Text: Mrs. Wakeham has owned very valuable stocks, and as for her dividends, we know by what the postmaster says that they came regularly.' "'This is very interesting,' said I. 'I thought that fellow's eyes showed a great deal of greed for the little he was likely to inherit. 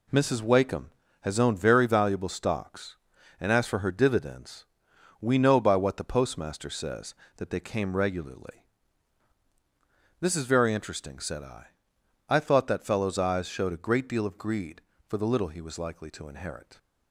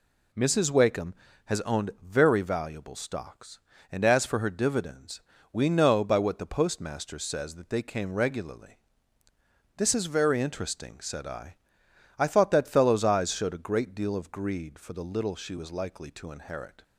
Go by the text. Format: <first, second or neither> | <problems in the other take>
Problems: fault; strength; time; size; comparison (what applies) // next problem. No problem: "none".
first | says "she" for "he"; at 15.3 s